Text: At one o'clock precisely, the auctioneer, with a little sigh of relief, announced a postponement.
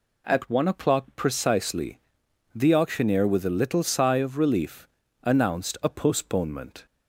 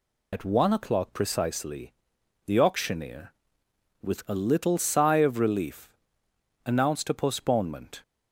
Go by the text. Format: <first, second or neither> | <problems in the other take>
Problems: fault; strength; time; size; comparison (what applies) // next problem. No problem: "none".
first | loses the start of "At"; at 0.3 s; 65 ms